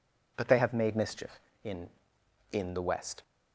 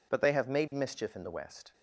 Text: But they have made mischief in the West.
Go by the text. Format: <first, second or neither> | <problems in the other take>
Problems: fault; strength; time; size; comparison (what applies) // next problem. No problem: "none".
second | says "in" twice; at 2.5 s